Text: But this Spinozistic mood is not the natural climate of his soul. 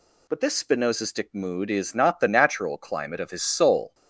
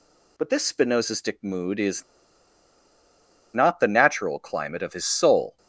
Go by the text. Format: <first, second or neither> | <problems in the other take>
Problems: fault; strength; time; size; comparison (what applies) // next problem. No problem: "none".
first | pauses between "is" and "not"; strong; at 2.0 s; 1.5 s long